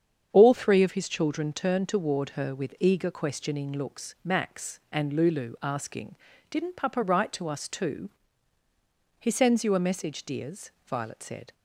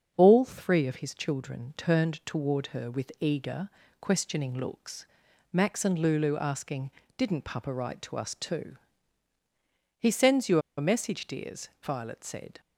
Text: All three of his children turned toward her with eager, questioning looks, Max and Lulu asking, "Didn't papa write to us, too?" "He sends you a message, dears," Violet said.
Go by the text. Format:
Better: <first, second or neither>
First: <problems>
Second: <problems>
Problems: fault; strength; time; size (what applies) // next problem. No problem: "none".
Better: first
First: starts louder than the rest; strong; until 1.3 s; 8 dB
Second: starts louder than the rest; strong; until 1.1 s; 7 dB // pauses between "you" and "a"; slight; at 10.5 s; 0.17 s long